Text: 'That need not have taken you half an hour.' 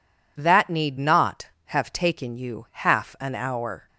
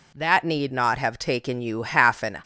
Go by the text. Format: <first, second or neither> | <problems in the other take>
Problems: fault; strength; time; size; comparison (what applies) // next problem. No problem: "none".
first | stops before "hour"; at 2.4 s